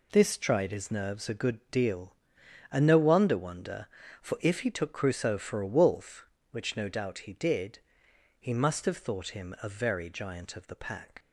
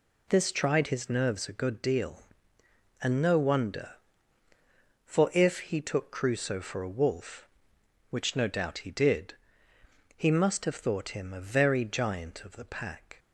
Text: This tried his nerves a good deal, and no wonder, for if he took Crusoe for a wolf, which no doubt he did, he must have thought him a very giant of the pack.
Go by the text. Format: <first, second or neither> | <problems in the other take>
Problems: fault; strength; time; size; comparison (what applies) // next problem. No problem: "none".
second | says "wonder" twice; at 3.3 s